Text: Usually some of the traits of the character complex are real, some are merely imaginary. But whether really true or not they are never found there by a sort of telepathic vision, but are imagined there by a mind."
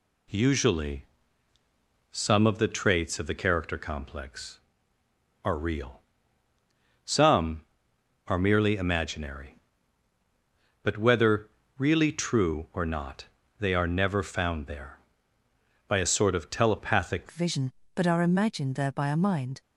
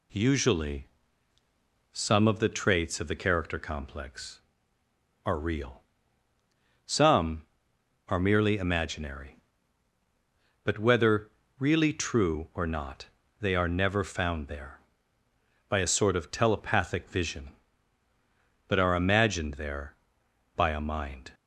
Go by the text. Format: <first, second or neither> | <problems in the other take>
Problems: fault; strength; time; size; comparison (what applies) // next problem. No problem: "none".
second | pauses between "Usually" and "some"; at 1.0 s; 1.0 s long; also in the second // pauses between "whether" and "really"; slight; at 11.4 s; 0.30 s long; slight in the second // pauses between "not" and "they"; slight; at 13.2 s; 0.34 s long; slight in the second // changes voice at "vision"; from 17.3 s on; 2.3 s long